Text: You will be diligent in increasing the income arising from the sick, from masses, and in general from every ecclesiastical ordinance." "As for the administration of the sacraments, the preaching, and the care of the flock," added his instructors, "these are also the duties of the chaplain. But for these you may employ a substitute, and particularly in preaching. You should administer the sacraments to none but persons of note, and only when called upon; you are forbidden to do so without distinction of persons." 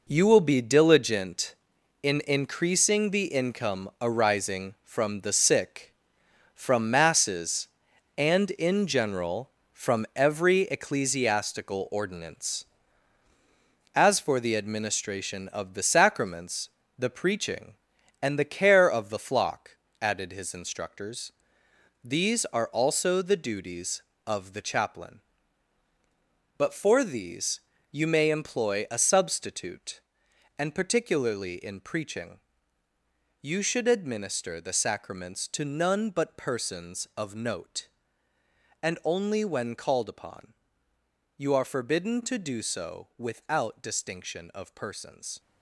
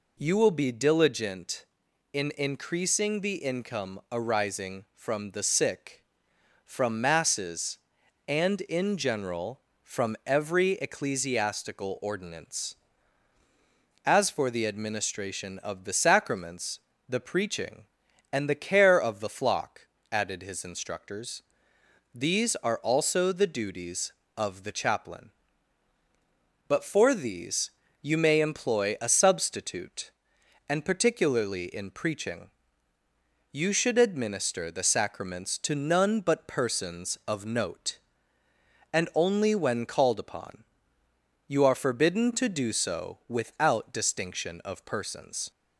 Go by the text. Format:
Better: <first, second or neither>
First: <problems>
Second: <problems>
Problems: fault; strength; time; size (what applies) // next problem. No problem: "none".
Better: second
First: gets quieter; strong; throughout; 9.5 dB // pauses between "these" and "you"; slight; at 27.5 s; 0.30 s long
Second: pauses between "these" and "you"; slight; at 27.7 s; 0.30 s long